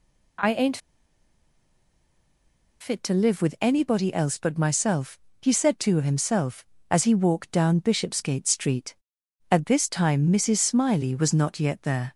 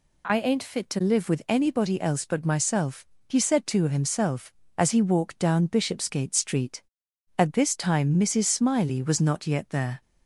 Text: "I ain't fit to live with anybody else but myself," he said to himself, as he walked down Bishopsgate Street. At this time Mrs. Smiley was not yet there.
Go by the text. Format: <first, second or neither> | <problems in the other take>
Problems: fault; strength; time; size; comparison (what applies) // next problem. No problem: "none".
second | pauses between "ain't" and "fit"; strong; at 0.7 s; 2.0 s long